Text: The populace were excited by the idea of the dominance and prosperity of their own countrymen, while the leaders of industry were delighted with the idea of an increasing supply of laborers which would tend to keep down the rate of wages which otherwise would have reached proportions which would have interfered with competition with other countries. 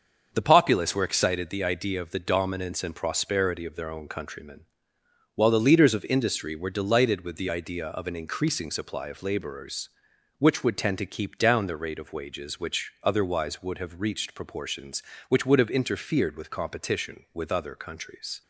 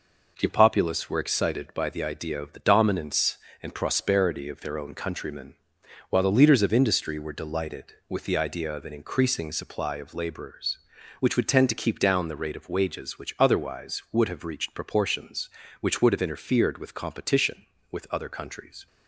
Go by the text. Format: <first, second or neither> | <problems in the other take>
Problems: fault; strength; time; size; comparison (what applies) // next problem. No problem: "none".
second | starts louder than the rest; until 1.3 s; 6.5 dB // skips "by"; at 1.4 s